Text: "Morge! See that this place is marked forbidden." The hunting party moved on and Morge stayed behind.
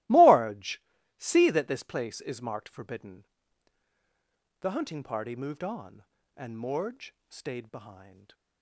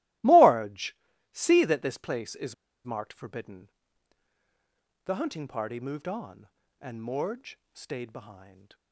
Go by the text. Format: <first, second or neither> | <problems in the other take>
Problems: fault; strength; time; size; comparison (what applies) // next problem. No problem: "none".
first | starts louder than the rest; strong; until 1.5 s; 17.5 dB; strong in the first // pauses between "is" and "marked"; slight; at 2.5 s; 0.32 s long // pauses between "Morge" and "stayed"; slight; at 7.5 s; 0.16 s long; slight in the first